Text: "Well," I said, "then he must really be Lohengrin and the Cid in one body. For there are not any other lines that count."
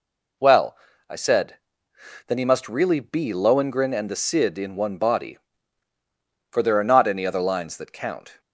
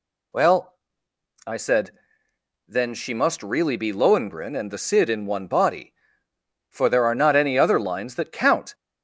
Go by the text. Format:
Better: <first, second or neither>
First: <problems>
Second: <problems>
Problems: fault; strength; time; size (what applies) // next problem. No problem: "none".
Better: first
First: none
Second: says "she" for "he"; at 2.9 s